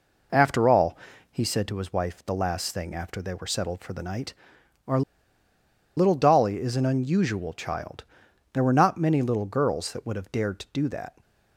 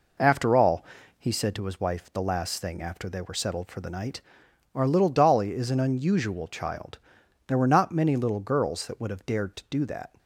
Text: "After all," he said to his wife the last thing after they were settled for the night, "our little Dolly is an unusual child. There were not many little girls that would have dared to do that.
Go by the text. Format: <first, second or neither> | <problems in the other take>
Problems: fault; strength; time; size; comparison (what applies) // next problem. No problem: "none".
second | pauses between "our" and "little"; noticeable; at 5.0 s; 0.96 s long